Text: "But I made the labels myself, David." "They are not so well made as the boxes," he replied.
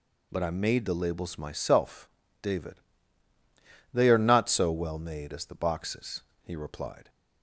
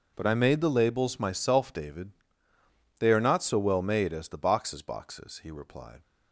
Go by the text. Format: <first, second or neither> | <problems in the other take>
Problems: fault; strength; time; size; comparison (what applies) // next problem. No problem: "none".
first | says "boxes" twice; at 4.8 s